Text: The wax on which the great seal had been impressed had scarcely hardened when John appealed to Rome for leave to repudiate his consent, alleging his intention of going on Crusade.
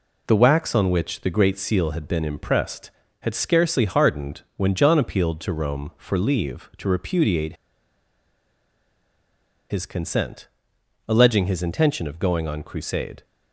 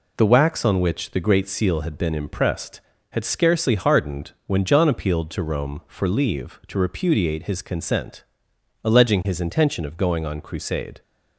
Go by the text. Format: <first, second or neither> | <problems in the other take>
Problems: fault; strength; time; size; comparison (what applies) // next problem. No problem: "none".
second | pauses between "repudiate" and "his"; strong; at 7.5 s; 2.1 s long